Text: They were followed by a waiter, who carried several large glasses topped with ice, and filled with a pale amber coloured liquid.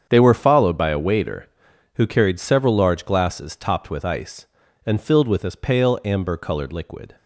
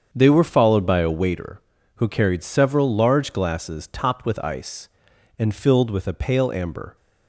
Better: first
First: starts louder than the rest; strong; until 1.1 s; 7.5 dB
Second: starts louder than the rest; strong; until 1.1 s; 7.5 dB // stops before "coloured liquid"; at 6.9 s

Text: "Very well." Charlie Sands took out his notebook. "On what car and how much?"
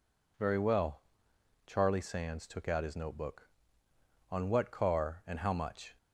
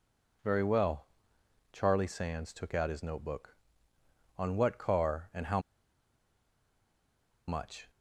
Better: first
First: none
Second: pauses between "how" and "much"; strong; at 5.5 s; 1.8 s long

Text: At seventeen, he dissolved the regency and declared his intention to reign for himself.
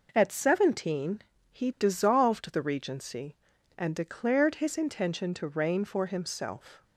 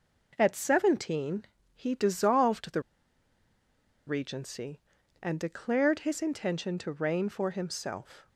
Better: first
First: none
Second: pauses between "the" and "regency"; strong; at 2.8 s; 1.2 s long

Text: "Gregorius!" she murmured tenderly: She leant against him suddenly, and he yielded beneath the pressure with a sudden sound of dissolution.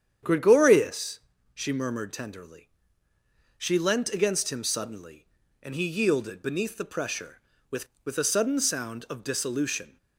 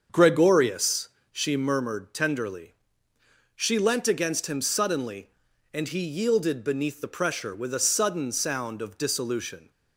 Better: second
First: starts louder than the rest; strong; until 1.5 s; 8.5 dB // says "with" twice; at 8.0 s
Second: starts louder than the rest; until 1.3 s; 6.5 dB

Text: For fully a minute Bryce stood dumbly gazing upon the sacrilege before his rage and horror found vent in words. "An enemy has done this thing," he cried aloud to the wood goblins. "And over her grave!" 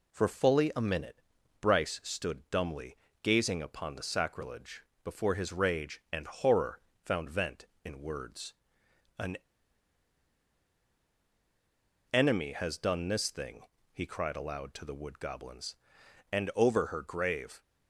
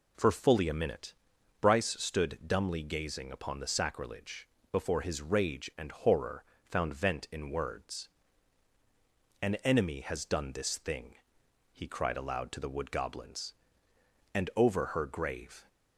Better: second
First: pauses between "minute" and "Bryce"; at 1.2 s; 0.40 s long // pauses between "dumbly" and "gazing"; slight; at 2.9 s; 0.24 s long // pauses between "sacrilege" and "before"; slight; at 4.8 s; 0.20 s long // pauses between "horror" and "found"; slight; at 6.8 s; 0.24 s long // pauses between "An" and "enemy"; strong; at 9.3 s; 2.7 s long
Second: pauses between "minute" and "Bryce"; noticeable; at 1.1 s; 0.48 s long // pauses between "sacrilege" and "before"; slight; at 4.4 s; 0.24 s long // pauses between "horror" and "found"; slight; at 6.4 s; 0.22 s long

